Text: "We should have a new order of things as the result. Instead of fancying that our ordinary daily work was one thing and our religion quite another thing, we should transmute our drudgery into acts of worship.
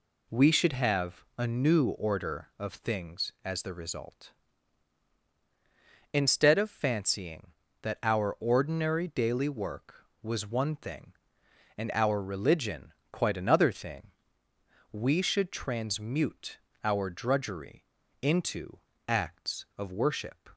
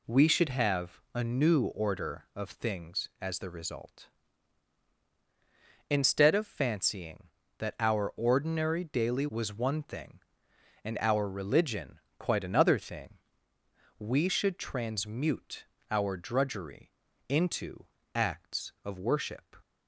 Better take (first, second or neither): first